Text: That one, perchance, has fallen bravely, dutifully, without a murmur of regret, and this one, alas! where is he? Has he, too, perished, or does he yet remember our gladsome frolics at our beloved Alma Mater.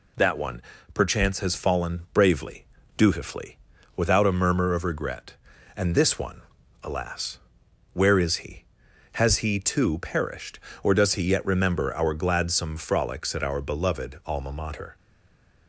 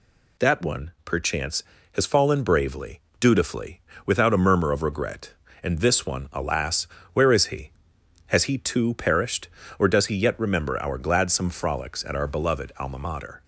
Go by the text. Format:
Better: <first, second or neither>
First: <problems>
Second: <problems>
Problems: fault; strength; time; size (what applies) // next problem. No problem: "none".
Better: second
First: stays silent after the last word; slight; from 14.9 s on; 0.7 s long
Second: none